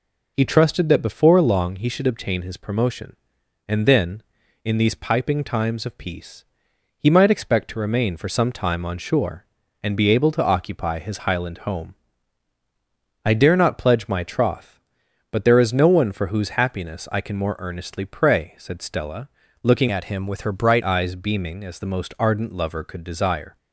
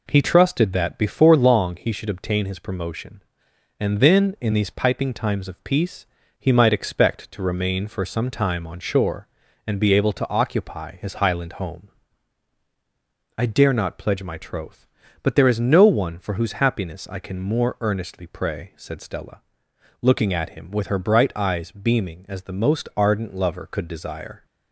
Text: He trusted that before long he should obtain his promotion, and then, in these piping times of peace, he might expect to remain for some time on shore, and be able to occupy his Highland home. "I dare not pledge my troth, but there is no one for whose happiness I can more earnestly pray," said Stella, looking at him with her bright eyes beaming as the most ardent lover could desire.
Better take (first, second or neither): second